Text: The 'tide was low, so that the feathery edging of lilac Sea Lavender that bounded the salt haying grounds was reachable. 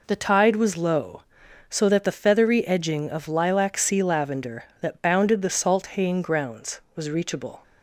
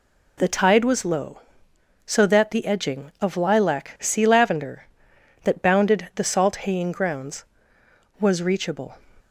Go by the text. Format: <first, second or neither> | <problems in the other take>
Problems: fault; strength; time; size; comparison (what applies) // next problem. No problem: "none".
first | skips "feathery"; at 2.6 s